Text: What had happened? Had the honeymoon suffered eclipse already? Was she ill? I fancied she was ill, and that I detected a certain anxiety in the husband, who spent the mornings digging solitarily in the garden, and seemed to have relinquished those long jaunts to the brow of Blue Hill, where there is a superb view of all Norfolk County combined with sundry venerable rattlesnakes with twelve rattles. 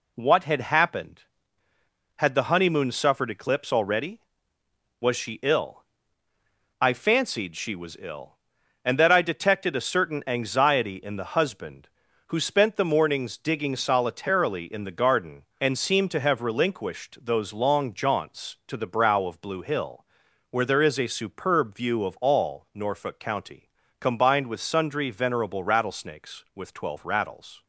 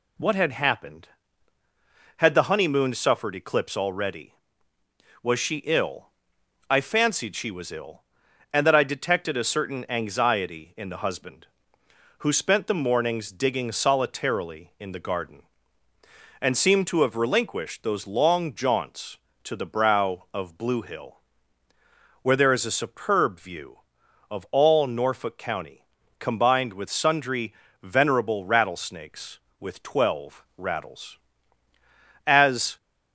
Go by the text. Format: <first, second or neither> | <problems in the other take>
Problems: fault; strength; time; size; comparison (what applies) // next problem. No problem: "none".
first | pauses between "County" and "combined"; slight; at 25.8 s; 0.34 s long; slight in the first // pauses between "sundry" and "venerable"; slight; at 27.5 s; 0.30 s long // goes on to say "As"; from 32.2 s on; 0.50 s long